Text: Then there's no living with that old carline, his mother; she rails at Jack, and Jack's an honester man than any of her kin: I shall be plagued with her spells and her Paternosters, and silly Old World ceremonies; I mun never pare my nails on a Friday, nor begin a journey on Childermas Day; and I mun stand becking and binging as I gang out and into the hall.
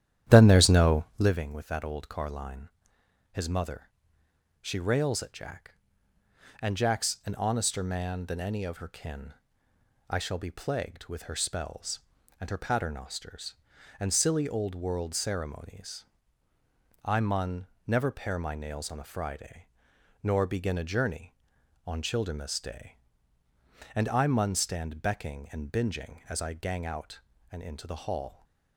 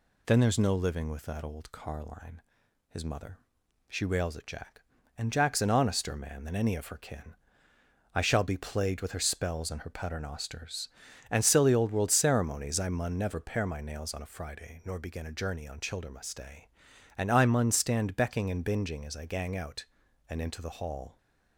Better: second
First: starts louder than the rest; strong; until 1.4 s; 11 dB // pauses between "mun" and "never"; slight; at 17.6 s; 0.18 s long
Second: none

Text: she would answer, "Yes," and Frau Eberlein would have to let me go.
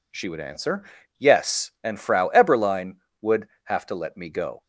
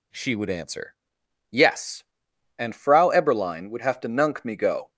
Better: first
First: none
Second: says "nunk" for "let"; at 4.0 s

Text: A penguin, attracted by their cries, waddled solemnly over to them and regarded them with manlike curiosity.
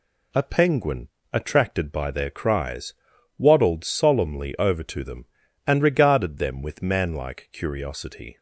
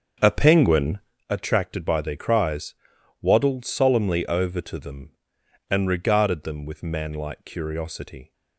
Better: first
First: none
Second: starts louder than the rest; until 1.2 s; 7 dB

